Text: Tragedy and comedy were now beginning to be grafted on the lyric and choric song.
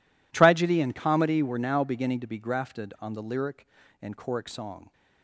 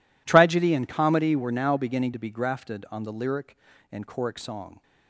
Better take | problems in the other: neither | none

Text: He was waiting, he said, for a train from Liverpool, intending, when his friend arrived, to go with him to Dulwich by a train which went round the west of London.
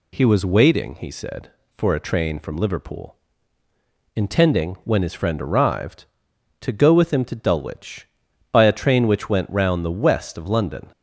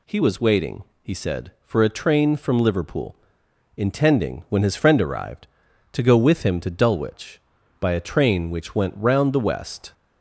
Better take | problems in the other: first | stops before "of London"; at 9.9 s

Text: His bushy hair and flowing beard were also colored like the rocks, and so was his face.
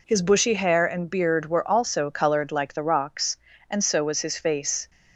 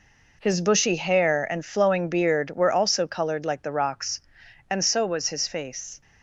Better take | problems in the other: second | skips "flowing"; at 1.0 s

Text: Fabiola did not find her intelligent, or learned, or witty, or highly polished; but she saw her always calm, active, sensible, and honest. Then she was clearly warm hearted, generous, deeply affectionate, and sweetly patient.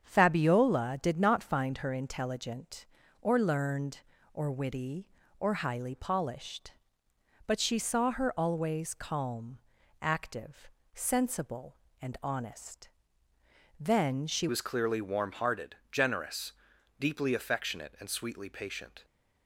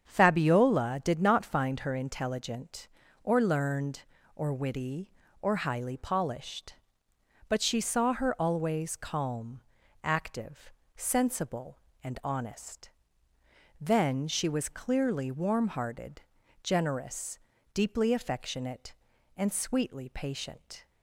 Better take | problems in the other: second | starts louder than the rest; strong; until 1.0 s; 7.5 dB; strong in the second // changes voice at "was"; from 14.4 s on; 4.6 s long

